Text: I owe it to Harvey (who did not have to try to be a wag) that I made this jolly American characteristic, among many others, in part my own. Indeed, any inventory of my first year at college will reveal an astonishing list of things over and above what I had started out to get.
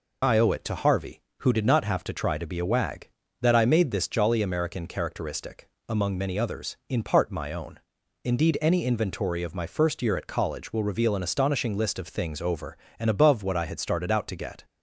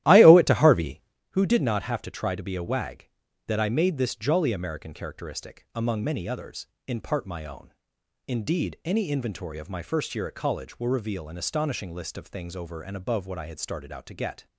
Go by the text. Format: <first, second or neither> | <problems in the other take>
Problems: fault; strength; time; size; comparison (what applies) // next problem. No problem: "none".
first | starts louder than the rest; strong; until 1.2 s; 14 dB